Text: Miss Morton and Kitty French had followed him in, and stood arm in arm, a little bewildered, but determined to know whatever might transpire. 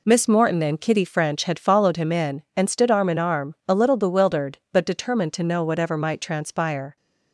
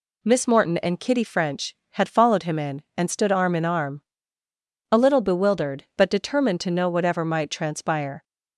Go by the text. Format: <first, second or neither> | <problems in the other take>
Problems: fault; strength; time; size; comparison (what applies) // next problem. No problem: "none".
second | gets quieter; strong; throughout; 7.5 dB